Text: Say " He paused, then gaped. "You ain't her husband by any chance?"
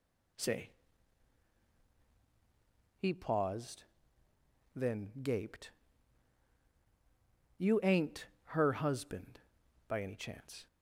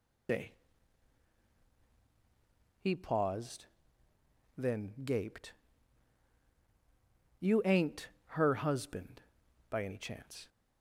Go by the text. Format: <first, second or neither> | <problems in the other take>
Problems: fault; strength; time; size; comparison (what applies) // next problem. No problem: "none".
first | loses the start of "Say"; at 0.2 s; 110 ms // pauses between "ain't" and "her"; slight; at 8.0 s; 0.20 s long; slight in the first